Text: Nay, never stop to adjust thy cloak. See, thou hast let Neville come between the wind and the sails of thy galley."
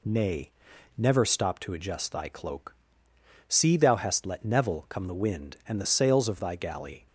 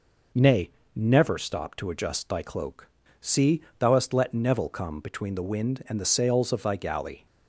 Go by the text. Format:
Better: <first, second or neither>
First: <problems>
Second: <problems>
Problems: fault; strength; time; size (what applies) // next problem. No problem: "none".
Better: second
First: skips "between"; at 5.0 s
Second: none